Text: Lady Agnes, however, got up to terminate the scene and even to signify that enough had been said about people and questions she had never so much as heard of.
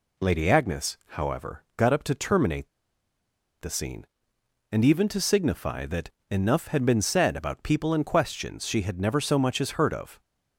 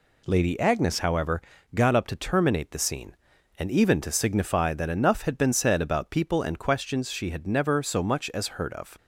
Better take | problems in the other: second | pauses between "terminate" and "the"; noticeable; at 2.6 s; 0.93 s long // pauses between "that" and "enough"; slight; at 6.1 s; 0.20 s long

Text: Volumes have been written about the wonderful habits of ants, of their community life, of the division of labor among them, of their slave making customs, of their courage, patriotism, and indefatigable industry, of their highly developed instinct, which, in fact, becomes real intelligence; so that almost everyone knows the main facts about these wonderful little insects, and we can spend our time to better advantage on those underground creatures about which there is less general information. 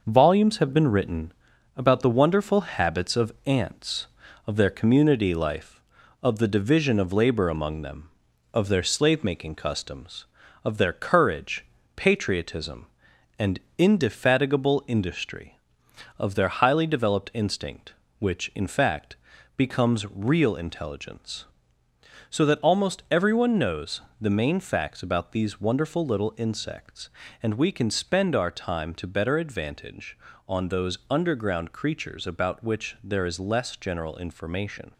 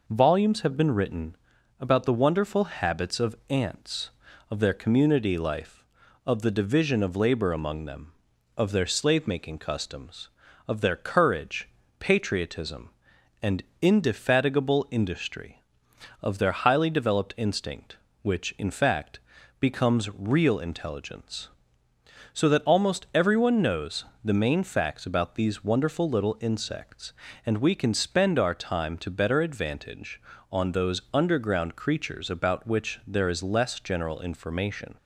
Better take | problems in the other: second | gets quieter; noticeable; throughout; 5 dB // pauses between "written" and "about"; noticeable; at 1.3 s; 0.46 s long; noticeable in the second // pauses between "and" and "indefatigable"; slight; at 13.6 s; 0.16 s long; slight in the second // pauses between "knows" and "the"; slight; at 24.0 s; 0.18 s long; slight in the second

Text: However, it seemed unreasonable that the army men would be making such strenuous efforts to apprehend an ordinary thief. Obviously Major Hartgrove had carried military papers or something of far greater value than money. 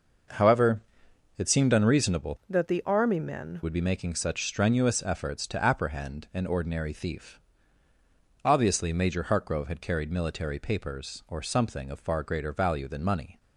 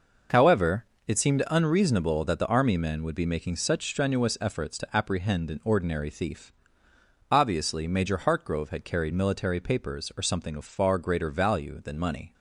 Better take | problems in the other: second | changes voice from "that" to "men"; from 2.4 to 3.6 s; 1.2 s long

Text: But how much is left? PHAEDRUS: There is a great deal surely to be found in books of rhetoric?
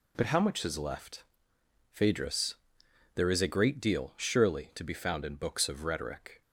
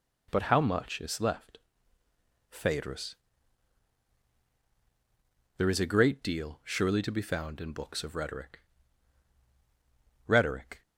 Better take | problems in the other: first | says "rhetoric" twice; at 10.2 s

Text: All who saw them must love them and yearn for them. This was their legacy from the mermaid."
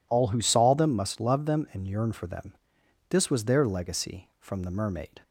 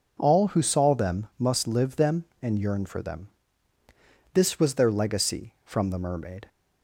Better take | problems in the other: first | says "live" for "love"; at 1.6 s

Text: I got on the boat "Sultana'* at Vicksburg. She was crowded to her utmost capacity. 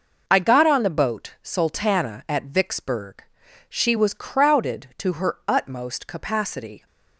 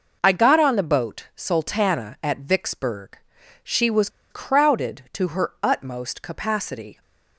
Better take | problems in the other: first | pauses between "was" and "crowded"; slight; at 4.0 s; 0.21 s long

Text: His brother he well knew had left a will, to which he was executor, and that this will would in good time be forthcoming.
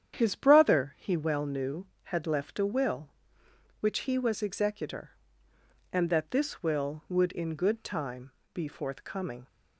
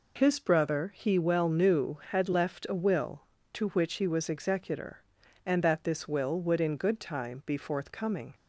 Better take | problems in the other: second | starts louder than the rest; strong; until 1.1 s; 9 dB // skips "to"; at 3.4 s // pauses between "time" and "be"; slight; at 8.3 s; 0.22 s long

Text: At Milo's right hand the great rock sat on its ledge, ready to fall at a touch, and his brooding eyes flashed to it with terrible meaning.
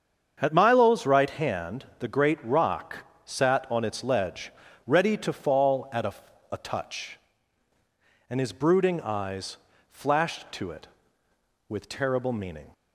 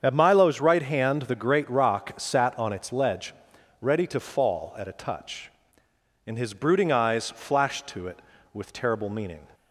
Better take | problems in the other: second | starts louder than the rest; strong; until 1.4 s; 7.5 dB; strong in the second // pauses between "rock" and "sat"; slight; at 3.0 s; 0.22 s long // says "a" twice; at 6.5 s // pauses between "eyes" and "flashed"; slight; at 9.5 s; 0.34 s long

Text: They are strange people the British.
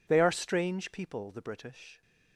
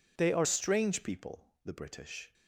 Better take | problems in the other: first | changes voice at "strange"; from 0.4 s on; 1.9 s long

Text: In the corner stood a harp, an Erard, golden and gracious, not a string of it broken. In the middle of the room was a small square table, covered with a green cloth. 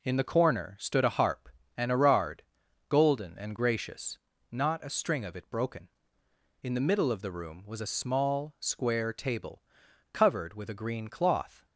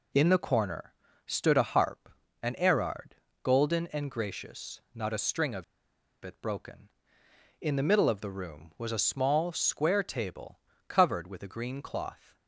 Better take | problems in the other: first | pauses between "corner" and "stood"; slight; at 0.9 s; 0.32 s long // pauses between "of" and "it"; noticeable; at 5.6 s; 0.60 s long

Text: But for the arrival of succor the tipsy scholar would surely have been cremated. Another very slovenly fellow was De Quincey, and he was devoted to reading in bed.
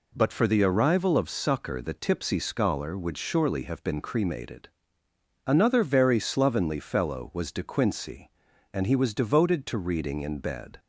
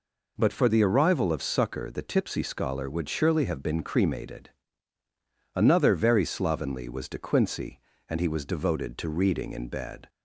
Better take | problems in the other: first | skips "fellow"; at 6.8 s

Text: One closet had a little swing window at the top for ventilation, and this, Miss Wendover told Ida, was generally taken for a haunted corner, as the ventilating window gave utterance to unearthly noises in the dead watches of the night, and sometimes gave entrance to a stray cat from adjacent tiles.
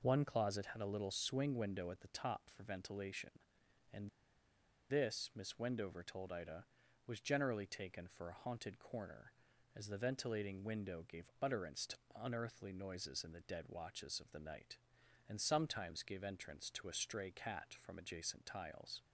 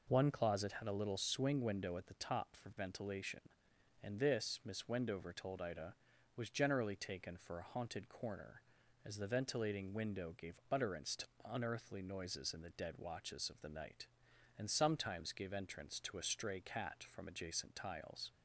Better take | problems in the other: second | pauses between "and" and "this"; noticeable; at 4.0 s; 0.81 s long // pauses between "to" and "unearthly"; slight; at 11.9 s; 0.24 s long; slight in the second

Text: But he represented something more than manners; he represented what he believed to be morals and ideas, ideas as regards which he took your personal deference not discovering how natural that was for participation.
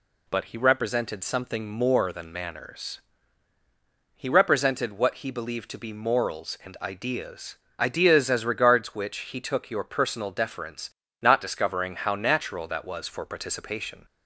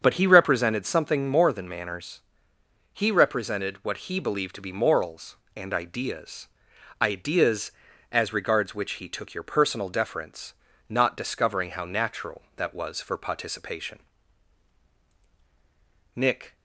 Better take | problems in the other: first | starts louder than the rest; strong; until 1.0 s; 7 dB // pauses between "deference" and "not"; slight; at 10.5 s; 0.36 s long; slight in the first // goes on to say "Nick"; slight; from 16.1 s on; 0.40 s long

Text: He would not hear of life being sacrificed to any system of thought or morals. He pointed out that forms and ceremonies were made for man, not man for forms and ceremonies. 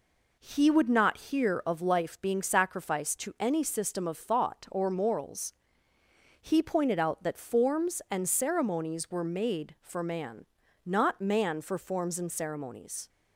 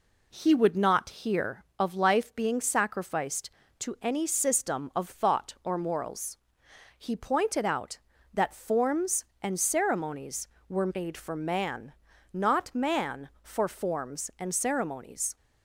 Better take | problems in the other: neither | none

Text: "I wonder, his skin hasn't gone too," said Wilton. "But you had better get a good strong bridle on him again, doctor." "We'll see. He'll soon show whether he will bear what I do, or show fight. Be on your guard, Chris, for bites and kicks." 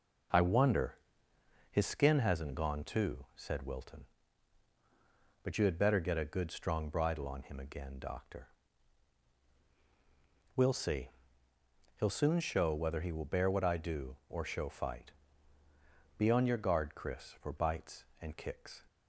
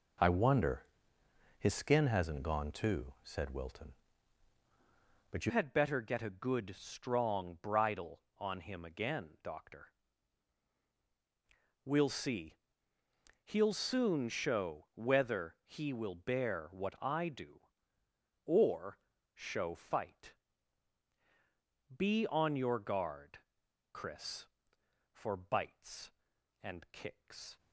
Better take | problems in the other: first | changes voice at "had"; from 5.4 s on; 22.1 s long // pauses between "or" and "show"; at 18.9 s; 0.38 s long

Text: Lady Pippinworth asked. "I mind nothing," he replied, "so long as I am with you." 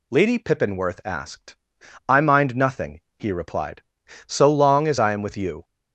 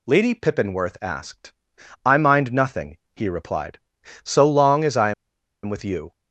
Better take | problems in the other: first | pauses between "I" and "am"; noticeable; at 5.1 s; 0.51 s long

